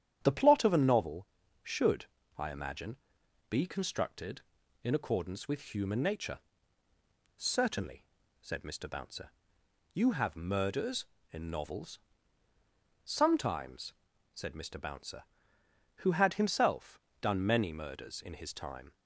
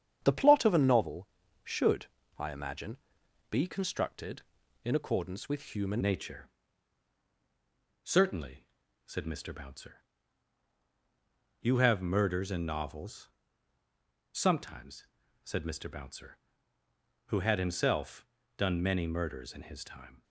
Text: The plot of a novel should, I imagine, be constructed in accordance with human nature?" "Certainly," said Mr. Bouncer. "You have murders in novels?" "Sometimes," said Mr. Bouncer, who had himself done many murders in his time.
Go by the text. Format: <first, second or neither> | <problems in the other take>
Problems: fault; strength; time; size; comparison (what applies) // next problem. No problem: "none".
first | starts louder than the rest; strong; until 1.2 s; 8.5 dB; strong in the first // changes voice at "nature"; from 6.0 s on; 14.2 s long // pauses between "himself" and "done"; slight; at 18.2 s; 0.32 s long; slight in the first